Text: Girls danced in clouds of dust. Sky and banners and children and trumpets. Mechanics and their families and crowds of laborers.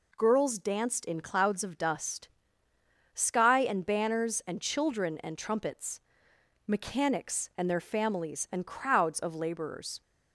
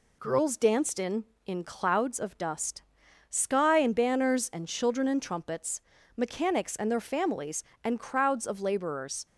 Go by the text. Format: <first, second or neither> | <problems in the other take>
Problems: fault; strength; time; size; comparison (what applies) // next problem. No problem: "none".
first | says "in" twice; at 1.4 s